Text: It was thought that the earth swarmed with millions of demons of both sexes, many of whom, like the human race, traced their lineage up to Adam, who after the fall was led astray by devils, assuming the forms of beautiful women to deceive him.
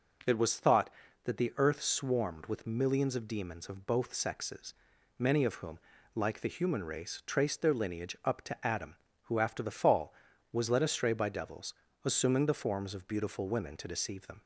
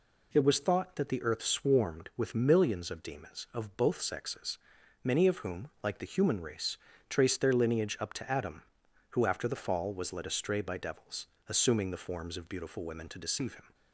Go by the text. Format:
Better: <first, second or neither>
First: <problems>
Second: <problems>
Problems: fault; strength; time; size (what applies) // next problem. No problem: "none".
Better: second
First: starts louder than the rest; noticeable; until 1.6 s; 6 dB // says "them" for "him"; at 14.2 s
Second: none